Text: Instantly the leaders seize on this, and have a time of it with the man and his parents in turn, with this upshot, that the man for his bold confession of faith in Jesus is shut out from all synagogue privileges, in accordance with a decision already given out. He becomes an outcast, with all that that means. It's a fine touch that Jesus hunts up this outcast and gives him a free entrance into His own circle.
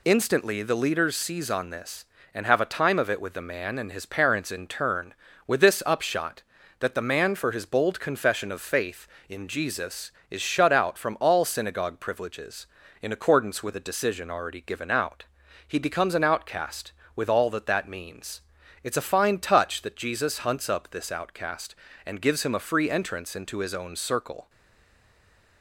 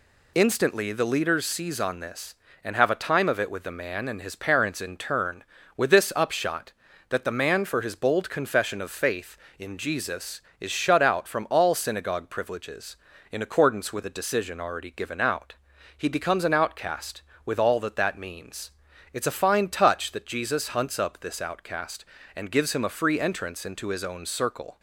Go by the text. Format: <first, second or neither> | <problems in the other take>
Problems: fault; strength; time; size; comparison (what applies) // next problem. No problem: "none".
second | stays silent after the last word; noticeable; from 24.4 s on; 1.2 s long